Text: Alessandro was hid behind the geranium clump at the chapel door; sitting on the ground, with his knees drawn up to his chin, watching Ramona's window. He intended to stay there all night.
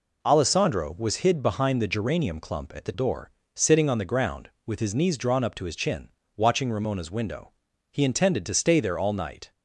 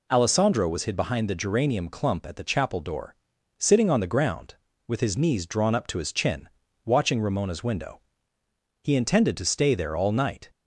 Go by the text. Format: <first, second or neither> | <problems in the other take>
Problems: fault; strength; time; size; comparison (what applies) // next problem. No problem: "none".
second | skips "chapel"; at 2.9 s